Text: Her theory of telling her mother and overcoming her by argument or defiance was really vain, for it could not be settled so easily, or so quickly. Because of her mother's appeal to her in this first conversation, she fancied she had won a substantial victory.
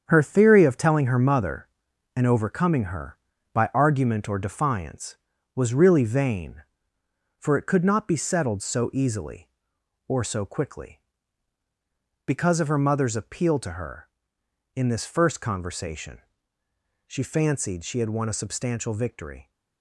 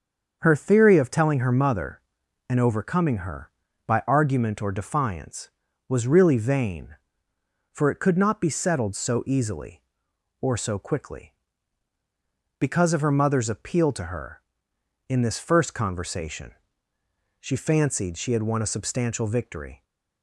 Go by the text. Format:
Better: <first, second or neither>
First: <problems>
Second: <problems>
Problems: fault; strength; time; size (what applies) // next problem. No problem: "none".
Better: second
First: gets quieter; strong; throughout; 7.5 dB // starts louder than the rest; strong; until 1.0 s; 7.5 dB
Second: starts louder than the rest; until 1.4 s; 7 dB